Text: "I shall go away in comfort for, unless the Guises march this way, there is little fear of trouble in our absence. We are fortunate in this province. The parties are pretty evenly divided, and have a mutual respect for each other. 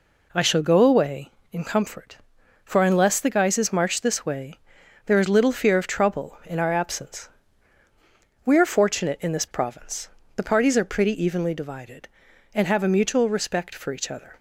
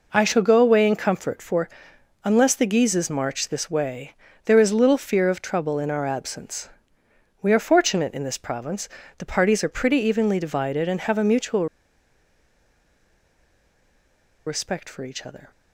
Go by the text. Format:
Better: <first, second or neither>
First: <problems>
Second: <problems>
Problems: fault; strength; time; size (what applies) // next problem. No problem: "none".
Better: first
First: none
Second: pauses between "mutual" and "respect"; strong; at 11.6 s; 2.8 s long